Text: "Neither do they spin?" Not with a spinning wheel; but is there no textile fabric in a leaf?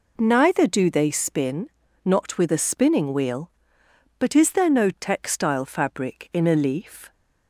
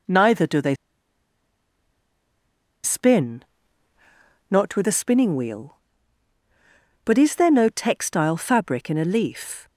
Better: first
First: none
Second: pauses between "they" and "spin"; strong; at 0.7 s; 2.0 s long

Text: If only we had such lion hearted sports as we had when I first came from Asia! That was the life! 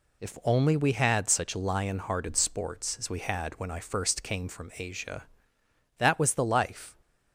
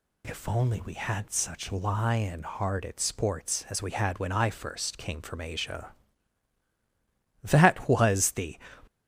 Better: first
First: none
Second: stops before "life"; at 8.8 s

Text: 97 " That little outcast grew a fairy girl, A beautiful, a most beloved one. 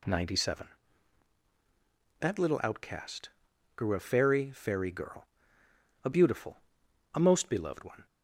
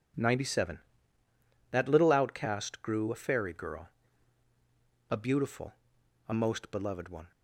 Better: second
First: pauses between "outcast" and "grew"; noticeable; at 3.2 s; 0.48 s long // says "fairy" twice; at 4.5 s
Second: none

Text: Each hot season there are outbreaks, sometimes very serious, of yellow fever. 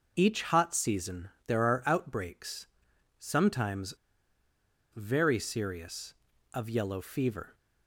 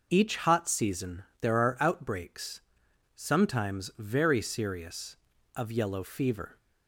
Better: second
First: pauses between "season" and "there"; slight; at 1.2 s; 0.18 s long // pauses between "sometimes" and "very"; at 3.9 s; 1.0 s long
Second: pauses between "season" and "there"; slight; at 1.2 s; 0.18 s long

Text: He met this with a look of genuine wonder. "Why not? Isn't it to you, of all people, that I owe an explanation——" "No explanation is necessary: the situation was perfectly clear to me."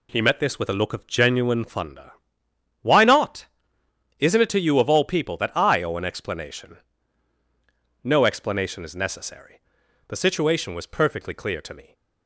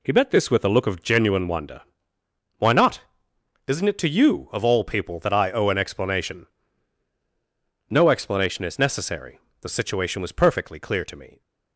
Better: second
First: says "thunder" for "wonder"; at 1.6 s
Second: none

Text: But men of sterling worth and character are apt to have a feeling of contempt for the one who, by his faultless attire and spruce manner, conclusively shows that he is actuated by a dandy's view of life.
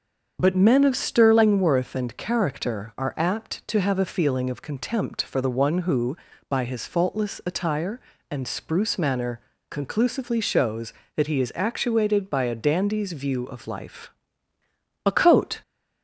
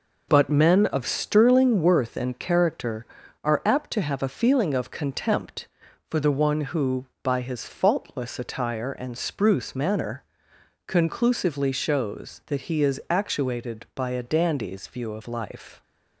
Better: second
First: starts louder than the rest; until 1.4 s; 7 dB // goes on to say "A coat"; from 15.0 s on; 0.56 s long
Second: none

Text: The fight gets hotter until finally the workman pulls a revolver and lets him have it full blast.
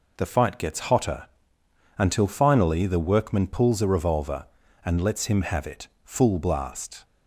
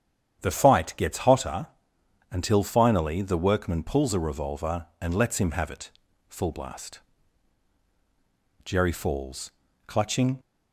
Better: first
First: pauses between "hotter" and "until"; noticeable; at 1.2 s; 0.72 s long // pauses between "it" and "full"; slight; at 5.8 s; 0.16 s long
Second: starts louder than the rest; strong; until 1.4 s; 9 dB // pauses between "hotter" and "until"; noticeable; at 1.6 s; 0.64 s long // pauses between "it" and "full"; at 5.8 s; 0.40 s long // goes on to say "Jerry falls clutching"; strong; from 8.6 s on; 1.7 s long

